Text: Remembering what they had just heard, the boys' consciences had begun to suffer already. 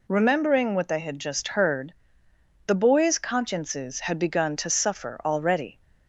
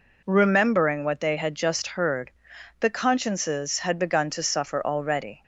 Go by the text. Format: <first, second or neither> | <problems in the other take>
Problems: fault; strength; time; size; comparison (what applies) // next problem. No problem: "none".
first | skips "boys"; at 2.9 s